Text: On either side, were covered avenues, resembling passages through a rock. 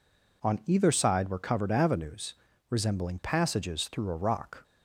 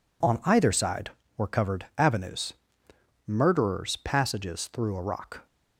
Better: first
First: none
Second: says "murderers" for "resembling"; at 3.2 s

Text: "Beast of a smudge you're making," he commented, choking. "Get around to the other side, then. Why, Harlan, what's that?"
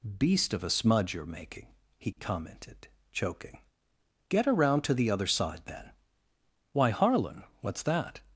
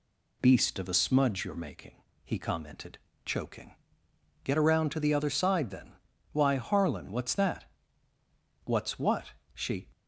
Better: first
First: none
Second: goes on to say "What's what She"; noticeable; from 8.6 s on; 1.2 s long

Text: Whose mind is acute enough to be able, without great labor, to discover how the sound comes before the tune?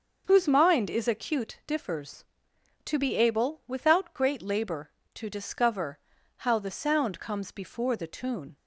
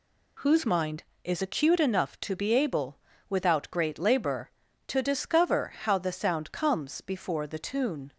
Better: second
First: starts louder than the rest; until 1.2 s; 6.5 dB // says "differs" for "enough"; at 1.6 s // pauses between "discover" and "how"; at 5.9 s; 0.40 s long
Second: none

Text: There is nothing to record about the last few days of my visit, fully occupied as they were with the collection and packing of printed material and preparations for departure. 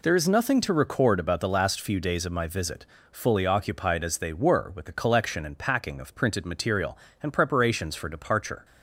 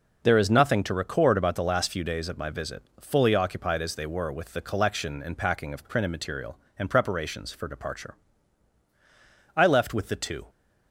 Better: first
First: none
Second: goes on to say "I left with the two"; noticeable; from 9.5 s on; 0.94 s long

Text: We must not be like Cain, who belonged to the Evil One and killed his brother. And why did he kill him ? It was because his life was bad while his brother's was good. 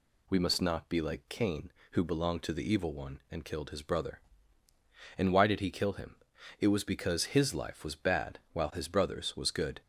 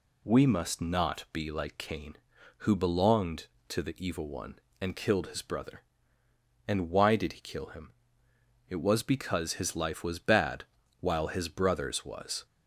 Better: first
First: none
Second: pauses between "bad" and "while"; slight; at 10.6 s; 0.36 s long // stops before "good"; at 12.4 s

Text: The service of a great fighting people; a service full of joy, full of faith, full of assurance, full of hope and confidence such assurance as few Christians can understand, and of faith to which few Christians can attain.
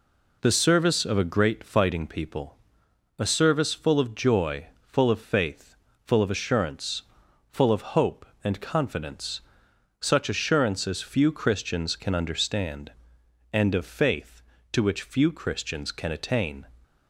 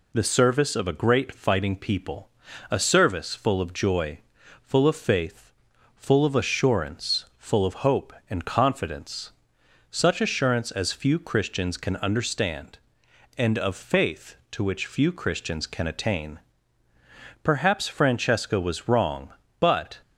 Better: first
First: pauses between "confidence" and "such"; noticeable; at 9.4 s; 0.62 s long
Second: pauses between "confidence" and "such"; noticeable; at 9.3 s; 0.58 s long // goes on to say "Perhaps Francesca was wrong but"; strong; from 17.4 s on; 2.5 s long

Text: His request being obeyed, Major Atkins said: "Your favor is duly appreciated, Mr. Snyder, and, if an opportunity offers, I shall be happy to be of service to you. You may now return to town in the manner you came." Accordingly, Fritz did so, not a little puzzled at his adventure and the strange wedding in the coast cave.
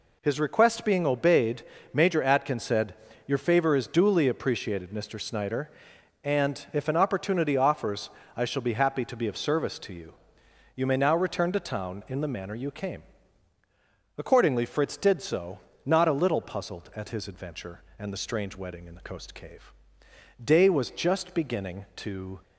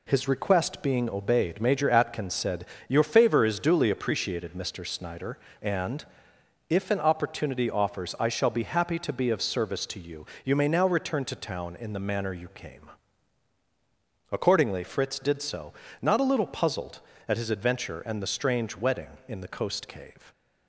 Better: second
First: goes on to say "Day was just beginning to"; strong; from 20.4 s on; 1.9 s long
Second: none

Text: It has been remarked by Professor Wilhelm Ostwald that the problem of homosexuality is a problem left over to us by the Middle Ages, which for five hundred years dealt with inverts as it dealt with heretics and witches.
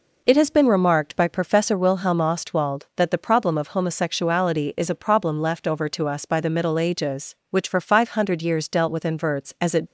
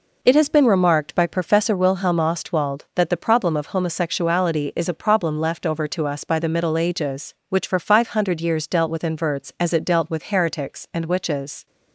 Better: second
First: stops before "dealt with heretics and witches"; at 9.8 s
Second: none

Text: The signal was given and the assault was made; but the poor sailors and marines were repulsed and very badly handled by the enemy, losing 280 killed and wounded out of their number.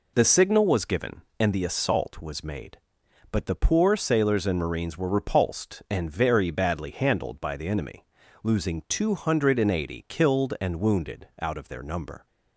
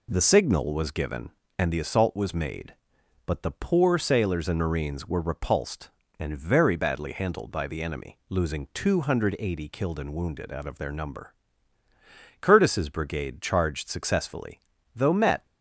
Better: first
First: none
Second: goes on to say "Curtis's brigade charged successfully though met"; strong; from 12.4 s on; 3.0 s long

